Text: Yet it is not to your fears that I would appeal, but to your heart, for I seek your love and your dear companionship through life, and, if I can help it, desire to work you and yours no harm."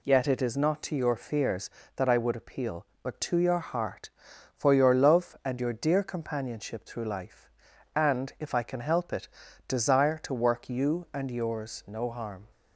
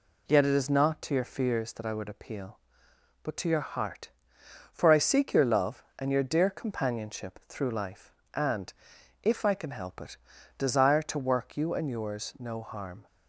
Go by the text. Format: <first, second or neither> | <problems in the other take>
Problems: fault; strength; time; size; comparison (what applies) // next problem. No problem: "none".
second | skips "I seek"; at 4.7 s